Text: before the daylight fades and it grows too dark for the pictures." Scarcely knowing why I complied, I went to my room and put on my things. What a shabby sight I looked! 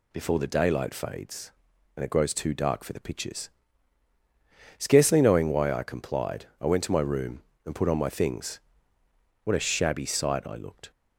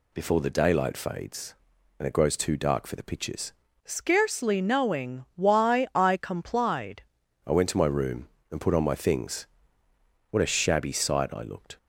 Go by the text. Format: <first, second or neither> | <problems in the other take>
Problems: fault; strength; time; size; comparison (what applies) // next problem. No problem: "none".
first | changes voice from "Scarcely" to "complied"; from 3.8 to 7.0 s; 3.2 s long